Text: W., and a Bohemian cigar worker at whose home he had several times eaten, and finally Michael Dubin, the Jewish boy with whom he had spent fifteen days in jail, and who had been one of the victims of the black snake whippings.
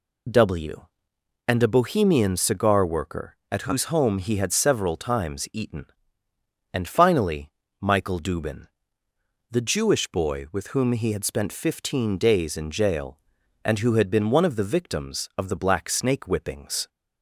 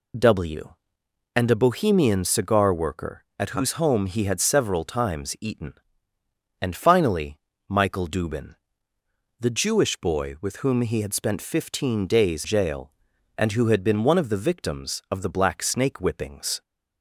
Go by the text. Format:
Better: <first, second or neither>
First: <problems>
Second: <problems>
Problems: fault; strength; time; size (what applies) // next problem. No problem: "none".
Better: first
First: pauses between "finally" and "Michael"; slight; at 7.4 s; 0.30 s long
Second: pauses between "finally" and "Michael"; slight; at 7.3 s; 0.30 s long // skips "in"; at 12.4 s